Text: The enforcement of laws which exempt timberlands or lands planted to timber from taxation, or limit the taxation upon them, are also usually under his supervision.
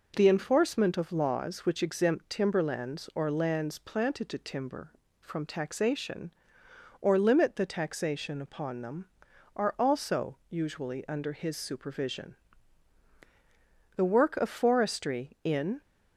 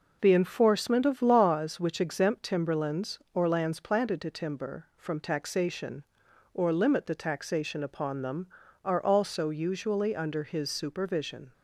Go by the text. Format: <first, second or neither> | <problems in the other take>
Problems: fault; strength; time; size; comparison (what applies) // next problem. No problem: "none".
second | goes on to say "The work of forestry in"; strong; from 13.9 s on; 1.8 s long